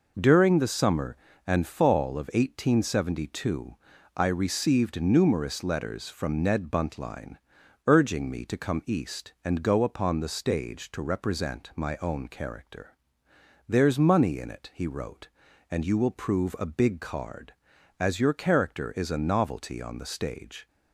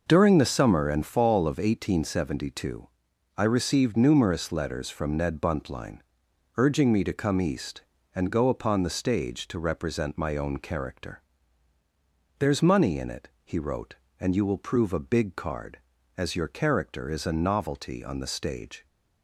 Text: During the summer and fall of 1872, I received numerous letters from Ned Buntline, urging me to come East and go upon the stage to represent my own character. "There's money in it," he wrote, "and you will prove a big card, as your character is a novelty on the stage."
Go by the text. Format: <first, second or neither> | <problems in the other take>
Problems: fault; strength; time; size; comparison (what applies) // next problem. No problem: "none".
neither | none